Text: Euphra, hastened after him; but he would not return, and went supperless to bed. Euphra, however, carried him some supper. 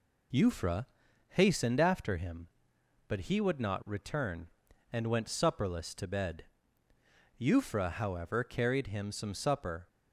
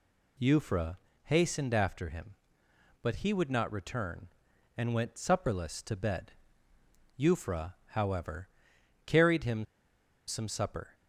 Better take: first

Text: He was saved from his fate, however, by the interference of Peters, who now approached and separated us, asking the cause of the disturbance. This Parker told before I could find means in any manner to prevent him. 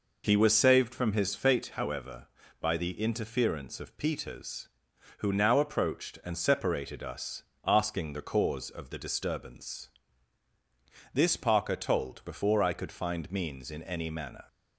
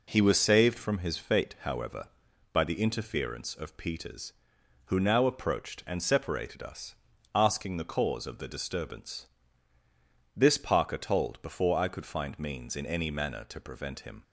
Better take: second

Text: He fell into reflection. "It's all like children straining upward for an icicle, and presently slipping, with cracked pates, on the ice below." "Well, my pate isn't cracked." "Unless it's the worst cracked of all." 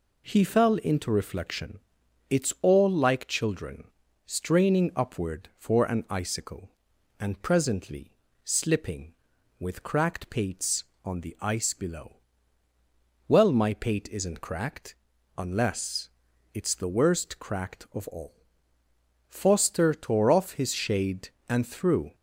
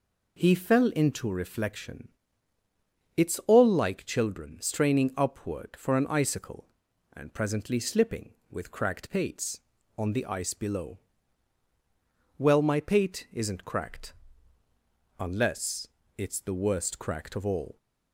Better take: second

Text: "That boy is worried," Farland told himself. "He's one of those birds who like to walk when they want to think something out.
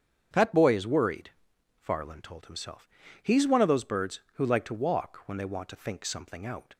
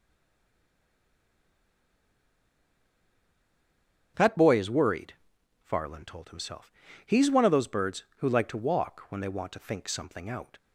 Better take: first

